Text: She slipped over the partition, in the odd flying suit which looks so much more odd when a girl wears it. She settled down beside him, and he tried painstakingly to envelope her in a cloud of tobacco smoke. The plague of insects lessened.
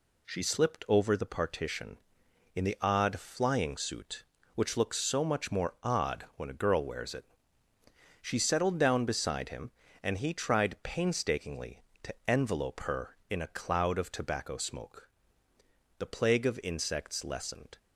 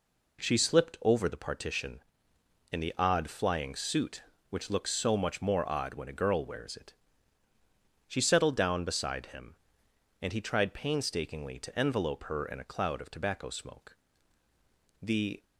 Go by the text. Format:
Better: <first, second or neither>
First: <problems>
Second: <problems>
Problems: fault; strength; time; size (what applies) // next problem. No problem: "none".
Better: first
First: none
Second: stops before "plague of insects lessened"; at 15.4 s